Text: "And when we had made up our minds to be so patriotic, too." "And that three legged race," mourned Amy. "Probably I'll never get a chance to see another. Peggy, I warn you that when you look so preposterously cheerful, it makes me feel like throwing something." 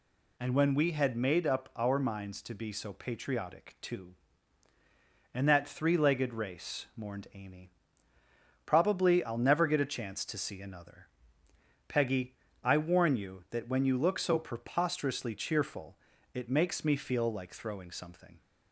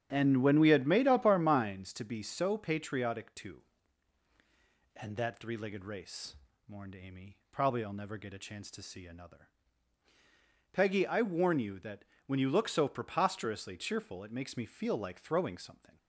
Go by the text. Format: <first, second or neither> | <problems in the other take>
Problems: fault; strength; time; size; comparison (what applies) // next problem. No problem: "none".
first | starts louder than the rest; strong; until 1.9 s; 9.5 dB // pauses between "that" and "when"; slight; at 12.0 s; 0.24 s long